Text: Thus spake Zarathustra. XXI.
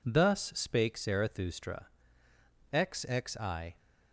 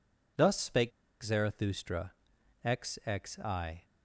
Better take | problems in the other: first | pauses between "spake" and "Zarathustra"; slight; at 0.9 s; 0.31 s long

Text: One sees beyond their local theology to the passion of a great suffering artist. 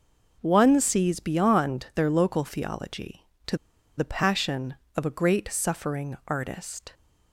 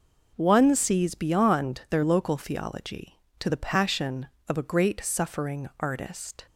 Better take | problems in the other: second | pauses between "to" and "the"; at 3.5 s; 0.40 s long

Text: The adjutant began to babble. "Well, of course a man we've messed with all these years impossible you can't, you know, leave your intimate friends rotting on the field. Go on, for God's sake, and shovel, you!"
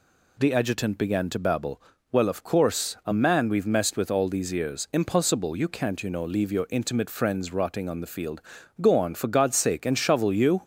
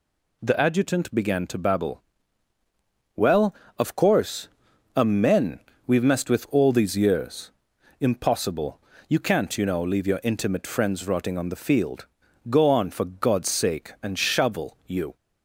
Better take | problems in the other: first | pauses between "course" and "a"; at 4.4 s; 0.44 s long // says "men" for "man"; at 5.0 s // pauses between "years" and "impossible"; noticeable; at 7.5 s; 0.48 s long // pauses between "impossible" and "you"; slight; at 8.7 s; 0.28 s long

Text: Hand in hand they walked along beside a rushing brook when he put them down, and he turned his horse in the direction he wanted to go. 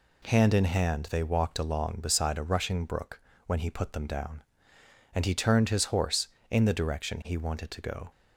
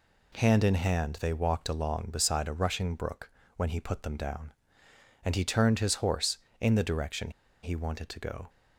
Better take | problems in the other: first | pauses between "brook" and "when"; slight; at 3.2 s; 0.26 s long; slight in the first // pauses between "direction" and "he"; slight; at 7.2 s; 0.33 s long

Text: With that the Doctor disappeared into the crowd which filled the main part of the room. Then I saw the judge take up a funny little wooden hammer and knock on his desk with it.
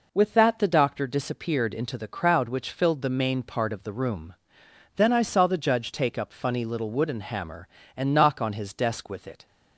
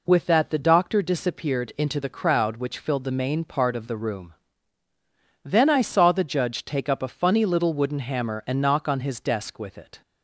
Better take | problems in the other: second | skips "a"; at 6.3 s

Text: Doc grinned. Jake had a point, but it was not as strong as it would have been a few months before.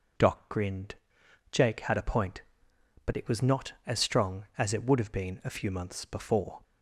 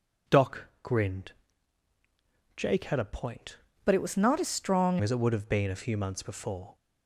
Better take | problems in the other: first | pauses between "Doc" and "grinned"; slight; at 0.6 s; 0.16 s long // changes voice from "but" to "strong"; from 3.8 to 4.9 s; 1.1 s long

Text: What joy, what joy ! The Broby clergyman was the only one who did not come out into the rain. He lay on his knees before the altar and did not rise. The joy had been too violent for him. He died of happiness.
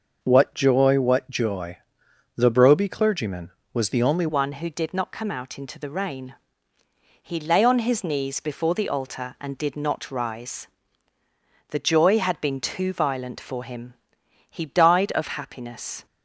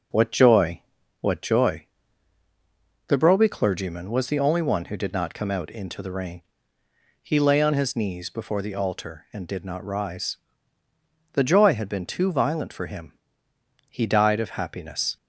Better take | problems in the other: second | changes voice at "one"; from 4.2 s on; 11.8 s long

